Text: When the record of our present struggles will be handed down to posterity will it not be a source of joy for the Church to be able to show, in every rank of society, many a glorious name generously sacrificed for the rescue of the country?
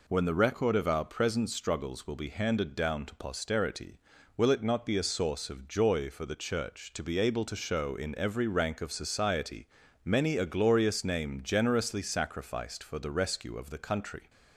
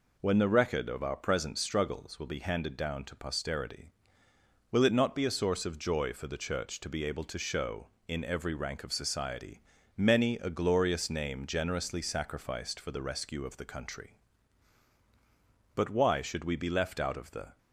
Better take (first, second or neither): first